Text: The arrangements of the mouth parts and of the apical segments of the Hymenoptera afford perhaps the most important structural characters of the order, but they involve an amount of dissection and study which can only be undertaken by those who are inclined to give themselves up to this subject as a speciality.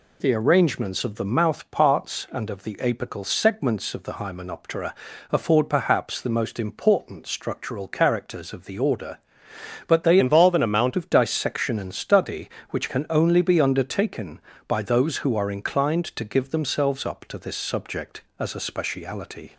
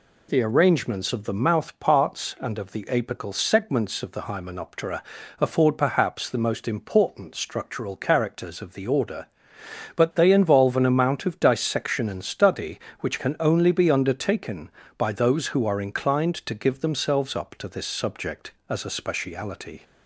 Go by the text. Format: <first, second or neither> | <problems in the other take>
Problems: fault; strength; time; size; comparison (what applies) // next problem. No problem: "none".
second | pauses between "Hymenoptera" and "afford"; at 4.9 s; 0.38 s long; also in the second // changes voice from "involve" to "amount"; from 10.1 to 10.9 s; 0.8 s long